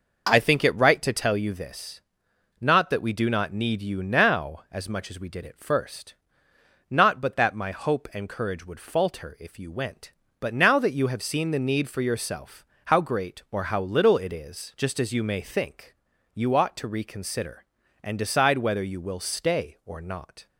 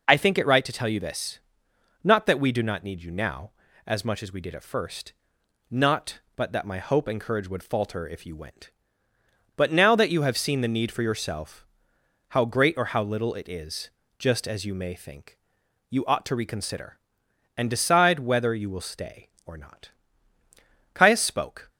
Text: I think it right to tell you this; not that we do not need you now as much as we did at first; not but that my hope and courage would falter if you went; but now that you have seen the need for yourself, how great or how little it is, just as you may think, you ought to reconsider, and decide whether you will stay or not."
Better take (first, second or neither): first